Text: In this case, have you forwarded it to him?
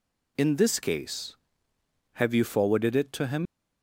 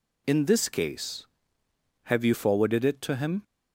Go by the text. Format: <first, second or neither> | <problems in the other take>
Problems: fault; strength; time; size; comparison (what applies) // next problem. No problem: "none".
second | leaves "him" unfinished; at 3.4 s; 85 ms